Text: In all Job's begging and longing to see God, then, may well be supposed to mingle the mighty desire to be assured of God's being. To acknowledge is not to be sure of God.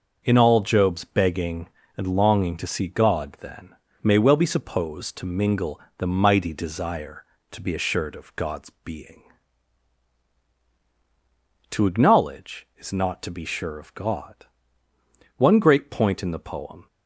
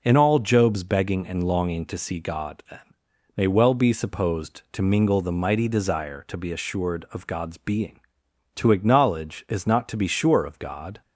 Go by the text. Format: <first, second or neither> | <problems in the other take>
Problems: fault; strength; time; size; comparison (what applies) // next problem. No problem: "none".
second | starts louder than the rest; noticeable; until 1.2 s; 6 dB // pauses between "mingle" and "the"; slight; at 5.8 s; 0.16 s long // goes on to say "One great point in the poem"; from 15.3 s on; 1.4 s long